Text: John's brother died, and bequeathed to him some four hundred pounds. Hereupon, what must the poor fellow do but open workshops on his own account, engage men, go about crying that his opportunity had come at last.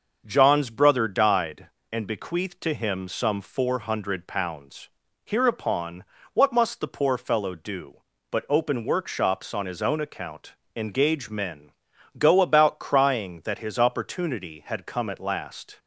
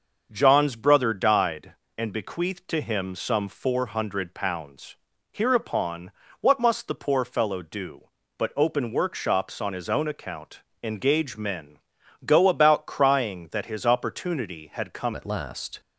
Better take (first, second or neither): first